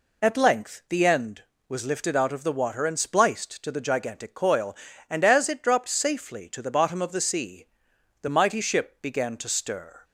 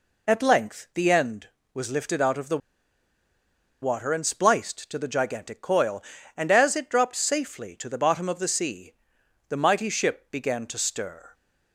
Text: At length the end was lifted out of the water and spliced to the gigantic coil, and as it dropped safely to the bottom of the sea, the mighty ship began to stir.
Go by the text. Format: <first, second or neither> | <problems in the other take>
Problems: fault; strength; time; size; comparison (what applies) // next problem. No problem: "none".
first | pauses between "the" and "water"; at 2.6 s; 1.2 s long